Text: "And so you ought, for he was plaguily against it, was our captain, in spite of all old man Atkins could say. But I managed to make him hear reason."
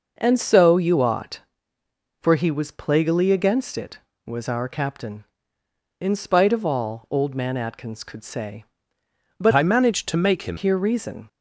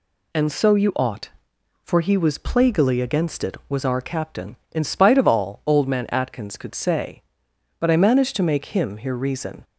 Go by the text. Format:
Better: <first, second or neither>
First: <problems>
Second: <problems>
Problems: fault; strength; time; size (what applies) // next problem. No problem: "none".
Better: second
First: changes voice from "I" to "him"; from 9.5 to 10.5 s; 1.0 s long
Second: none